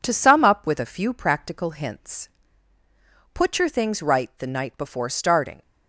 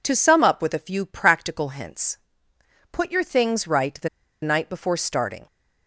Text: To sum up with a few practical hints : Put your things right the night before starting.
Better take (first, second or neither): first